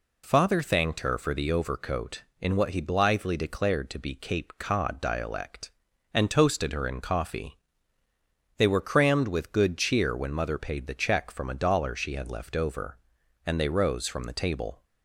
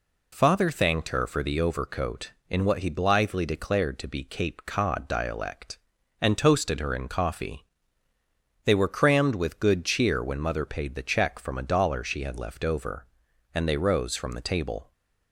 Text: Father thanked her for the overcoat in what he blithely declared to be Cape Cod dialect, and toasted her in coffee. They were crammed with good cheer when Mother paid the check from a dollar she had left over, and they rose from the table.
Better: neither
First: none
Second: none

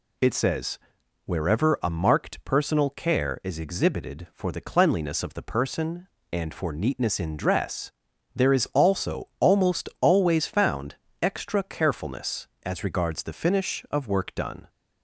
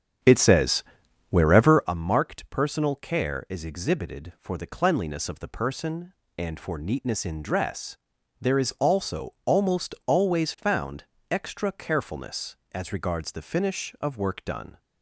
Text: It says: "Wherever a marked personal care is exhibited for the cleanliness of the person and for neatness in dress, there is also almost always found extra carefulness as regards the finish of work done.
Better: first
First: pauses between "found" and "extra"; slight; at 10.9 s; 0.26 s long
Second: starts louder than the rest; strong; until 2.0 s; 8.5 dB // pauses between "found" and "extra"; slight; at 11.0 s; 0.26 s long

